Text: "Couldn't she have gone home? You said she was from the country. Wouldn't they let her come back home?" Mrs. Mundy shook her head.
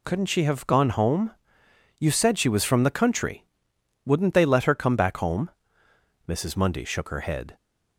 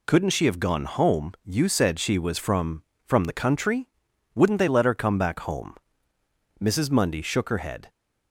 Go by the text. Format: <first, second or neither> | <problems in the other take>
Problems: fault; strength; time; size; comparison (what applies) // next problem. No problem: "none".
first | says "from" twice; at 3.0 s